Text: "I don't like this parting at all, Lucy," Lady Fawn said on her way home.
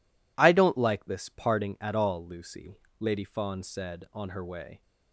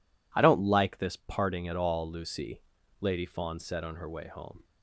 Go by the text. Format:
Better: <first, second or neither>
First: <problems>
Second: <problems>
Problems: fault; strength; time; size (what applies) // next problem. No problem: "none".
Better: second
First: stops before "home"; at 4.8 s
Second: none